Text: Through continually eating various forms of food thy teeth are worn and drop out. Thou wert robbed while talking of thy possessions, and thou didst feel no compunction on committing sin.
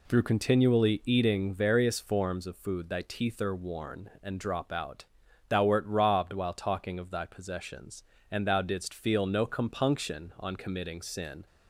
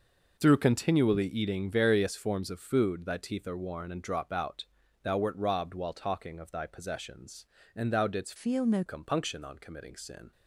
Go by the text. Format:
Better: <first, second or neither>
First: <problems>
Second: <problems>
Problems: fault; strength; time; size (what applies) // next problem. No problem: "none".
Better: first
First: none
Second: changes voice from "feel" to "no"; from 8.3 to 8.8 s; 0.5 s long